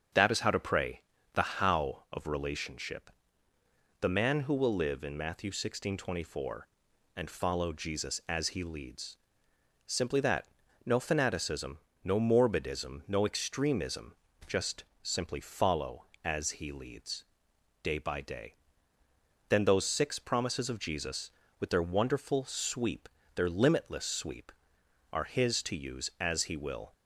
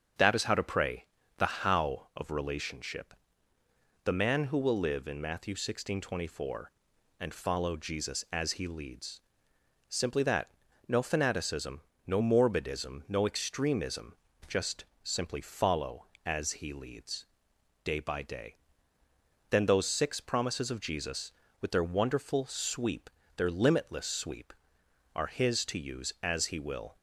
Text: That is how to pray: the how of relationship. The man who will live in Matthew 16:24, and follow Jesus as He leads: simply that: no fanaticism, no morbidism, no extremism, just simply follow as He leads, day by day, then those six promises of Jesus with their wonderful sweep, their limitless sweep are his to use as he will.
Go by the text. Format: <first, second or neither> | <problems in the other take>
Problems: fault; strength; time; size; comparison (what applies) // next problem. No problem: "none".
neither | starts louder than the rest; strong; the same in both // pauses between "just" and "simply"; slight; the same in both